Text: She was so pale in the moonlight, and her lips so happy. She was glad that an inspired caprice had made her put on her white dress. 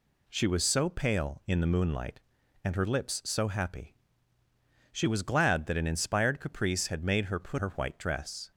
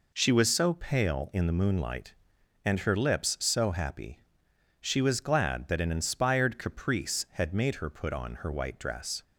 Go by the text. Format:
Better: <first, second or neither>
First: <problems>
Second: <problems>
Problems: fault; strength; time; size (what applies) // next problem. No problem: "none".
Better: second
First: skips "on"; at 7.5 s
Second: none